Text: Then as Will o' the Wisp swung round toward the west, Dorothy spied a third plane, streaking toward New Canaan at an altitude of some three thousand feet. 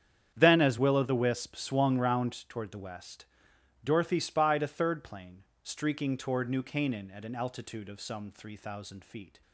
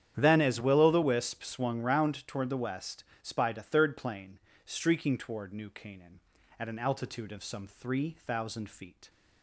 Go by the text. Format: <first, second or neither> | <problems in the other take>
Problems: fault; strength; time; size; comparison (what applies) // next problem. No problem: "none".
first | starts louder than the rest; strong; until 1.1 s; 9.5 dB; strong in the first // skips "Dorothy"; at 3.1 s